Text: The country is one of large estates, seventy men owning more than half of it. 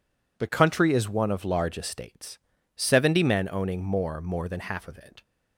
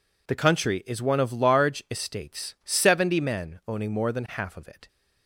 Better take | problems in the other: second | says "more" twice; at 4.2 s

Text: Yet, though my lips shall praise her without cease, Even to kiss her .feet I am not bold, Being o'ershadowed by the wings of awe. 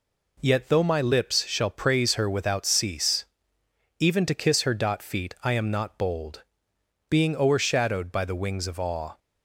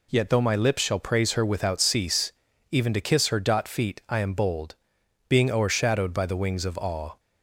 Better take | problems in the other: first | skips "not"; at 4.3 s

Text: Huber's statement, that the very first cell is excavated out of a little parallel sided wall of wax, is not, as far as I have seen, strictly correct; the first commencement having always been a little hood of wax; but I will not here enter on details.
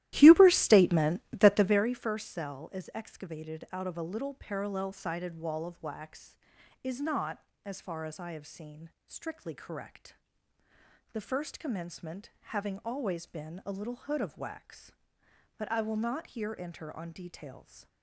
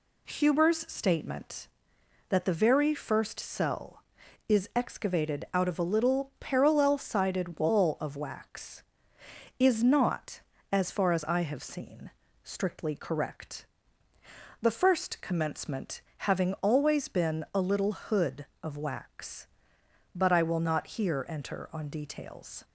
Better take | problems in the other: second | starts louder than the rest; strong; until 2.0 s; 14.5 dB // pauses between "commencement" and "having"; slight; at 12.2 s; 0.24 s long; slight in the second

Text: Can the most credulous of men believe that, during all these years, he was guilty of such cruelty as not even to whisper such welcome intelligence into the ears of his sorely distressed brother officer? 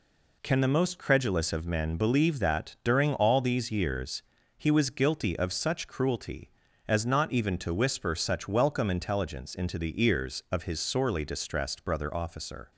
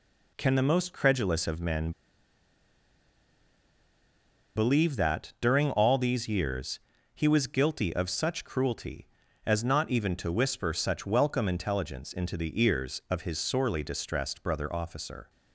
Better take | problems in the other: first | pauses between "men" and "believe"; strong; at 1.9 s; 2.6 s long

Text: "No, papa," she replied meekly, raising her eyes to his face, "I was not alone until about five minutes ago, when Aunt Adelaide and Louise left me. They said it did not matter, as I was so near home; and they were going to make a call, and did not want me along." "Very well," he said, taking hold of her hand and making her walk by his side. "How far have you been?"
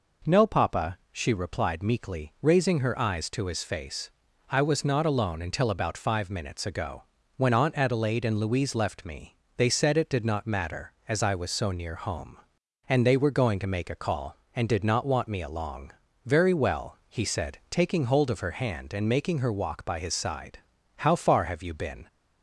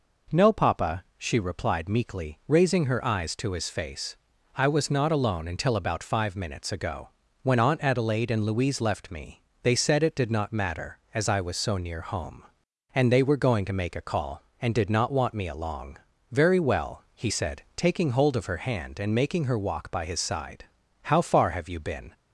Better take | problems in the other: neither | none

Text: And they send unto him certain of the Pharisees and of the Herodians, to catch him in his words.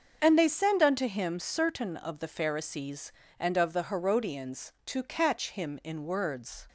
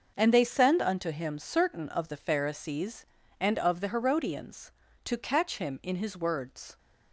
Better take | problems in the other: second | starts louder than the rest; until 1.2 s; 6.5 dB; noticeable in the second // skips "his"; at 6.0 s

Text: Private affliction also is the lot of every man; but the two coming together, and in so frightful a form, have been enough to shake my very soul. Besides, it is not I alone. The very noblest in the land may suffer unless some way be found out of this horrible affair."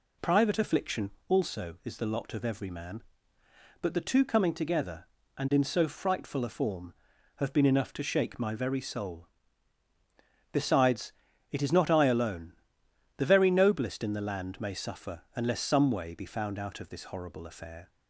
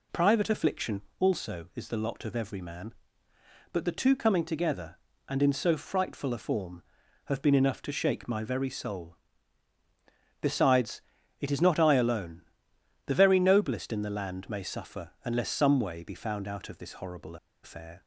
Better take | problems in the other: first | pauses between "affliction" and "also"; slight; at 1.0 s; 0.18 s long; slight in the first // pauses between "horrible" and "affair"; slight; at 17.3 s; 0.27 s long

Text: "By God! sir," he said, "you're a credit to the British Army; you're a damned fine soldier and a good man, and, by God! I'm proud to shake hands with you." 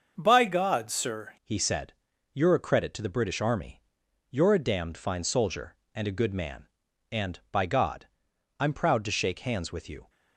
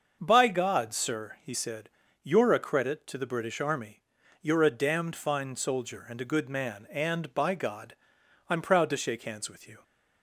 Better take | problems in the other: second | starts louder than the rest; until 1.1 s; 6.5 dB; also in the second // changes voice at "he"; from 1.4 s on; 8.6 s long

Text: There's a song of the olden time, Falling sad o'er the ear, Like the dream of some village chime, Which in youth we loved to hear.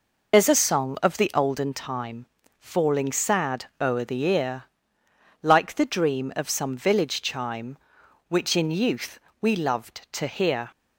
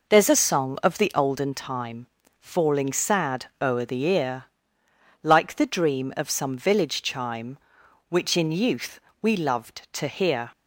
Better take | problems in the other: second | loses the start of "There's"; at 0.3 s; 50 ms // pauses between "youth" and "we"; slight; at 9.1 s; 0.24 s long; slight in the second

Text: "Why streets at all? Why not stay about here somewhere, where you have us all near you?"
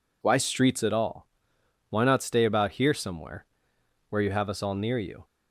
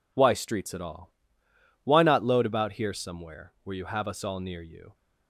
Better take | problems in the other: first | says "load" for "stay"; at 2.2 s

